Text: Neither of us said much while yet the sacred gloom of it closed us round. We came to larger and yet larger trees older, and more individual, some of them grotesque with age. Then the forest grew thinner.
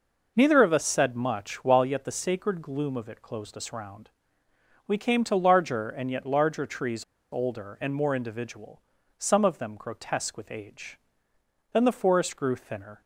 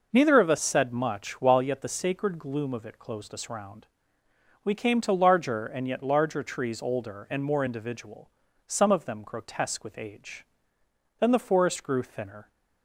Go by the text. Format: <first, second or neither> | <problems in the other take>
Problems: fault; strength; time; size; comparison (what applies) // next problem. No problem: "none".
second | pauses between "trees" and "older"; slight; at 7.0 s; 0.28 s long